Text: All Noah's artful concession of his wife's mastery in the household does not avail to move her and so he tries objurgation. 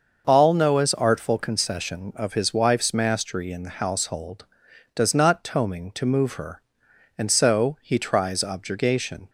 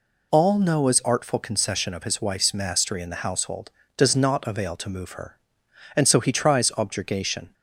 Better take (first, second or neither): second